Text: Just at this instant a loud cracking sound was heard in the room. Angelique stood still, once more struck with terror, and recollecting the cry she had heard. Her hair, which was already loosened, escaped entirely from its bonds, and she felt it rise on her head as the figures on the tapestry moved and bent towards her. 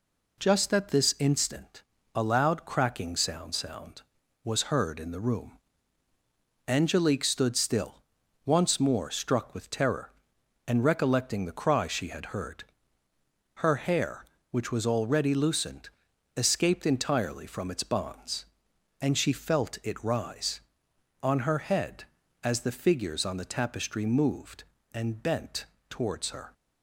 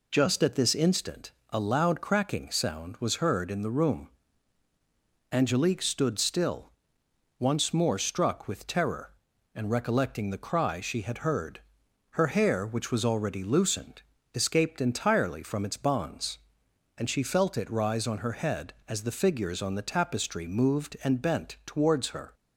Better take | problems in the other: second | pauses between "instant" and "a"; slight; at 1.8 s; 0.32 s long; slight in the second // says "sound" twice; at 3.5 s // pauses between "bent" and "towards"; slight; at 25.6 s; 0.24 s long

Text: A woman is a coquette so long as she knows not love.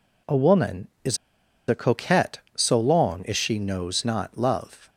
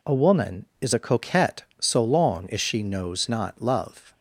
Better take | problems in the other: second | pauses between "is" and "a"; noticeable; at 1.1 s; 0.52 s long

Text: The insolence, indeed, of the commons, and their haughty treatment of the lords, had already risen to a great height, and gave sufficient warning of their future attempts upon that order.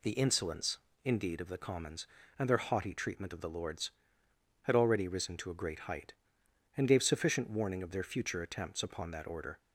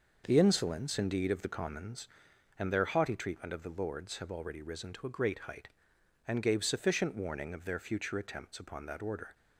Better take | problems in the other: first | says "have" for "had"; at 4.1 s

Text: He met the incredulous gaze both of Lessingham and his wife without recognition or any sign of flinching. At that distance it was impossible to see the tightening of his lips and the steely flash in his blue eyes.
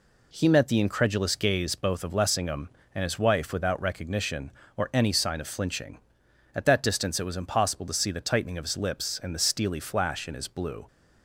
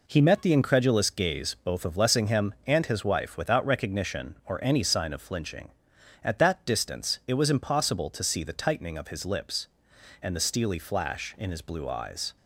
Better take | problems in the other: second | stops before "eyes"; at 10.8 s

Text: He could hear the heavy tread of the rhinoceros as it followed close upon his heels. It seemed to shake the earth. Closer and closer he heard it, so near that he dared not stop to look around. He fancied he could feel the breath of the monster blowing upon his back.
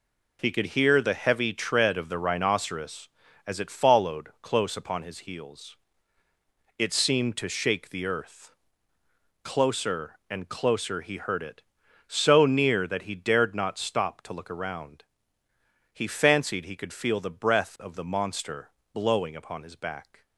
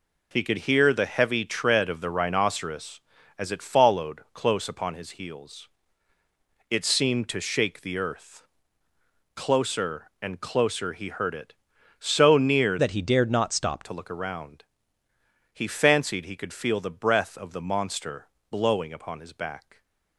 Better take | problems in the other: first | changes voice from "that" to "stop"; from 12.7 to 13.8 s; 1.1 s long // pauses between "monster" and "blowing"; slight; at 18.2 s; 0.22 s long; slight in the first

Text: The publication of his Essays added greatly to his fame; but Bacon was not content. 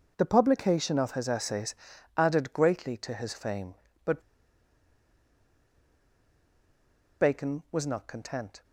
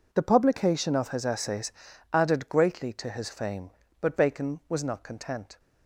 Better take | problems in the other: second | pauses between "Essays" and "added"; at 1.7 s; 0.42 s long; also in the second // pauses between "but" and "Bacon"; strong; at 4.2 s; 3.0 s long

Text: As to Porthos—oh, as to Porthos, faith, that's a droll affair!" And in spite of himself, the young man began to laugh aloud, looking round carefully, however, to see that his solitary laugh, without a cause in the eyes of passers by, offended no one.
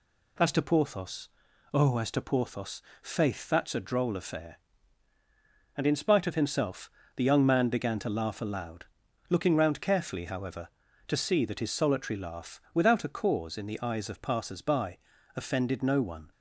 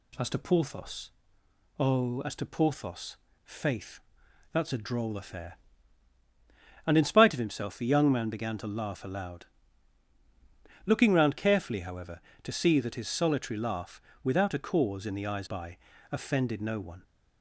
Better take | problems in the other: first | skips "of passers"; at 15.4 s

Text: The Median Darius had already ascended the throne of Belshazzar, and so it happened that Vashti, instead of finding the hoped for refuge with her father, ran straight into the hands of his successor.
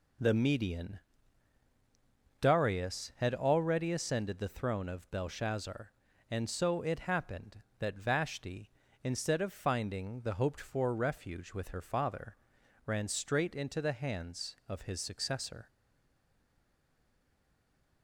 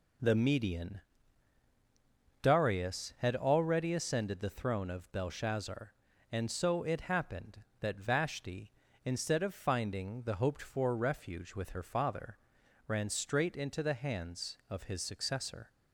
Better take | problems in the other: second | pauses between "Median" and "Darius"; strong; at 0.9 s; 1.4 s long; strong in the second // stays silent after the last word; from 15.6 s on; 2.4 s long

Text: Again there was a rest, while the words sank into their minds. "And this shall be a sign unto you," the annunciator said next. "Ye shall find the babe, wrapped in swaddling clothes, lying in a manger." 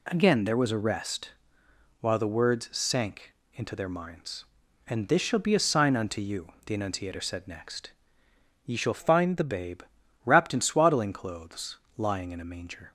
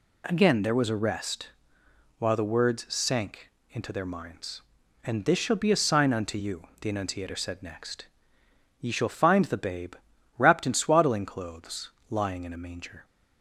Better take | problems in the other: second | pauses between "sank" and "into"; slight; at 3.3 s; 0.20 s long; slight in the second // changes voice from "find" to "the"; from 8.9 to 9.4 s; 0.5 s long

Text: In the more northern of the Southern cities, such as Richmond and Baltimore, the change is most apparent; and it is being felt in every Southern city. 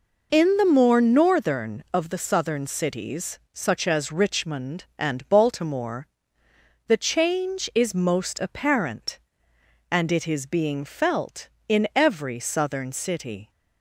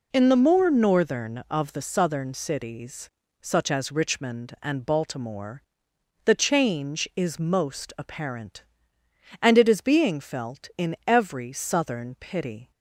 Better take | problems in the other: first | says "pity" for "city"; at 12.1 s

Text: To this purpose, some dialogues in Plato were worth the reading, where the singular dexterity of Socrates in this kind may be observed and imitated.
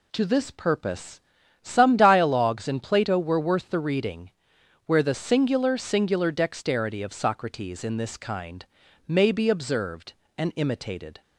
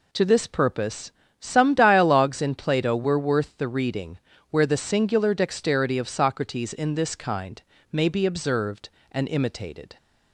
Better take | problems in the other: second | says "singular" twice; at 5.7 s // pauses between "kind" and "may"; at 8.6 s; 0.40 s long; slight in the second

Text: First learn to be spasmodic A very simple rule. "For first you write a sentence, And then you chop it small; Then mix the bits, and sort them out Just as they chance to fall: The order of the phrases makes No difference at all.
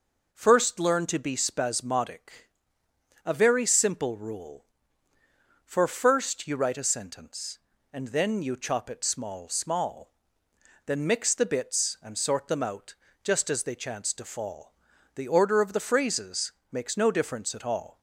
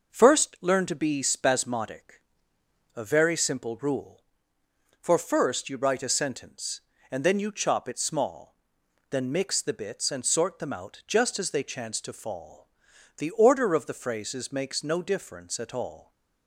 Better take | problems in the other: second | pauses between "spasmodic" and "A"; noticeable; at 2.4 s; 0.76 s long; noticeable in the second // says "small" twice; at 9.4 s // pauses between "out" and "Just"; slight; at 12.9 s; 0.30 s long // pauses between "phrases" and "makes"; slight; at 16.5 s; 0.18 s long

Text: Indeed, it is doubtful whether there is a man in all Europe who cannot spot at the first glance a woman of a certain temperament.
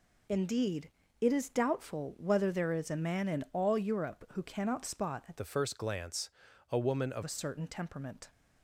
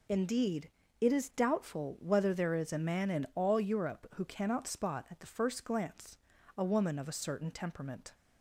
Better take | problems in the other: second | changes voice from "the" to "of"; from 5.3 to 7.2 s; 1.9 s long // pauses between "glance" and "a"; at 6.2 s; 0.40 s long; also in the second

